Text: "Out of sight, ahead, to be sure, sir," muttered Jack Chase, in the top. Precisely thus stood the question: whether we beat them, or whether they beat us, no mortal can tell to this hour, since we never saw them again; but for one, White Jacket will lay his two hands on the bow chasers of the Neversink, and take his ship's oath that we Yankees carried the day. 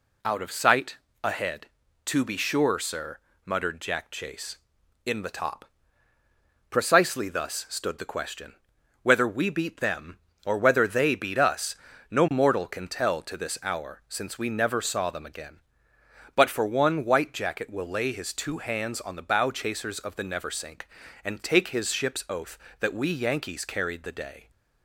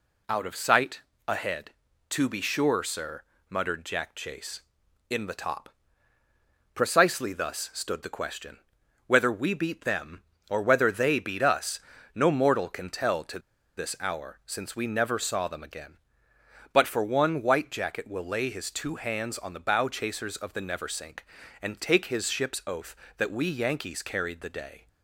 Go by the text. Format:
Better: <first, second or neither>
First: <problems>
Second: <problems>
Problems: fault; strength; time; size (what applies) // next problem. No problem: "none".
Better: first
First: none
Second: pauses between "to" and "this"; at 13.3 s; 0.38 s long